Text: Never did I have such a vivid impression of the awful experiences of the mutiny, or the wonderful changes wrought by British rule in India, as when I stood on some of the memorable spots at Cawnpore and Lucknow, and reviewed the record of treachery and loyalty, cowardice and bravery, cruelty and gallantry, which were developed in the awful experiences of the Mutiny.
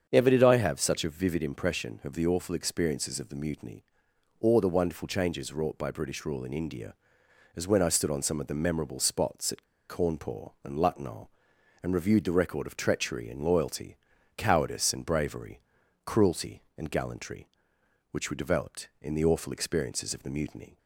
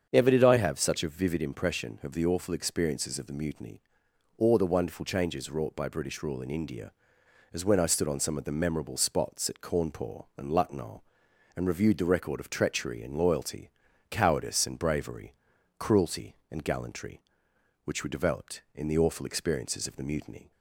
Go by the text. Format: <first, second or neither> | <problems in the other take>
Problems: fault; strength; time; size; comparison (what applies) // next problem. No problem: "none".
second | starts louder than the rest; strong; until 1.1 s; 7.5 dB; strong in the second // pauses between "at" and "Cawnpore"; slight; at 9.6 s; 0.24 s long